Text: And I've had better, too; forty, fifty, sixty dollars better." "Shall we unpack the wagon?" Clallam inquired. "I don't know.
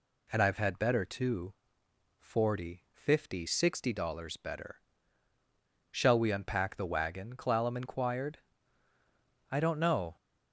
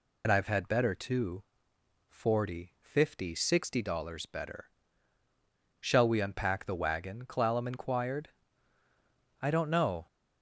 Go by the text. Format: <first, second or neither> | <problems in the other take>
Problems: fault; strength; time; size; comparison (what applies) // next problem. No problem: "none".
first | loses the start of "And"; at 0.2 s; 60 ms